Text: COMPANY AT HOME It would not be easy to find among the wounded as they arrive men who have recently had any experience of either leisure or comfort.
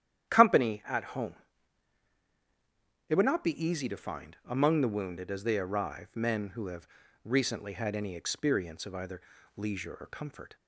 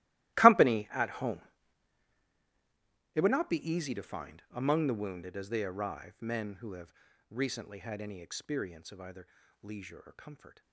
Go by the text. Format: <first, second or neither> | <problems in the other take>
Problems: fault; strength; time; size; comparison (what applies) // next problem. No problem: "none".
first | gets quieter; strong; throughout; 19.5 dB // starts louder than the rest; strong; until 3.2 s; 16.5 dB; strong in the first // pauses between "HOME" and "It"; strong; at 1.4 s; 1.7 s long; strong in the first // pauses between "have" and "recently"; at 6.9 s; 0.38 s long; also in the first // pauses between "either" and "leisure"; slight; at 9.2 s; 0.34 s long; slight in the first